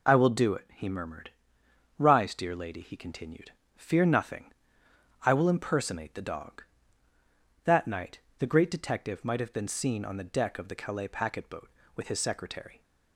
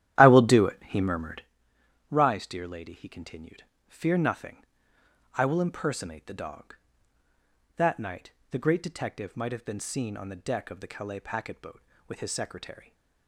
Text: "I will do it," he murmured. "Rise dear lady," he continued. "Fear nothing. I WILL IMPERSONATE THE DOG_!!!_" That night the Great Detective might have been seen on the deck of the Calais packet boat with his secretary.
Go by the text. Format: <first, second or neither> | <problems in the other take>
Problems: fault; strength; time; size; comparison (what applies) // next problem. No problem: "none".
first | starts louder than the rest; strong; until 1.5 s; 12 dB // pauses between "night" and "the"; slight; at 8.2 s; 0.22 s long; slight in the first